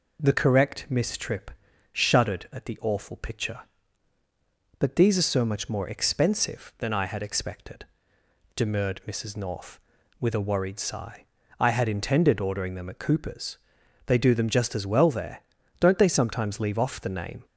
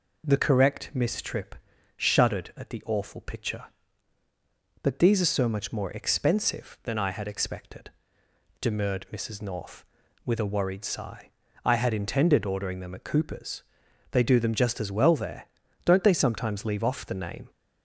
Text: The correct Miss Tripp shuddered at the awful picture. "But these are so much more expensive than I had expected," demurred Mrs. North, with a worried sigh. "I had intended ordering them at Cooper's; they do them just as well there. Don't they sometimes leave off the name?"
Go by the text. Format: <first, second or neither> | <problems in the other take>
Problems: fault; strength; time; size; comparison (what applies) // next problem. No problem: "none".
neither | pauses between "Tripp" and "shuddered"; the same in both